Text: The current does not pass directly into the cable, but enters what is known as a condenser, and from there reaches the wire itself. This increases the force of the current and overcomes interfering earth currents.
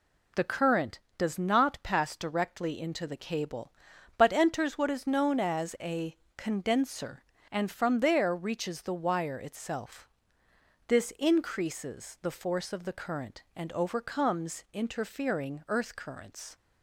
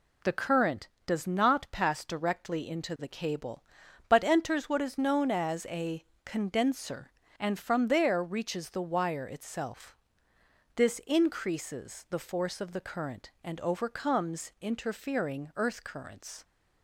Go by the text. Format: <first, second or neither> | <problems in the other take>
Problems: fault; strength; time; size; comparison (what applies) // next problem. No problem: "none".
neither | pauses between "a" and "condenser"; slight; the same in both